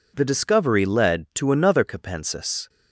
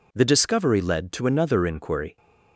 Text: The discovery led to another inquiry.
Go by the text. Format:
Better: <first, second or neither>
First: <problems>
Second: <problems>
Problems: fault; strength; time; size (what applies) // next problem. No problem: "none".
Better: second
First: says "capensis" for "inquiry"; at 1.8 s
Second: none